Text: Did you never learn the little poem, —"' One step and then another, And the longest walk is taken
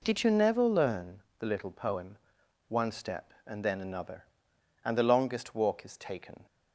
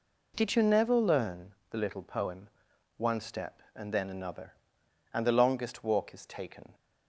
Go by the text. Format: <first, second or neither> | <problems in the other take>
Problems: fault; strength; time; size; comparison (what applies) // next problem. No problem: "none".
neither | pauses between "learn" and "the"; slight; the same in both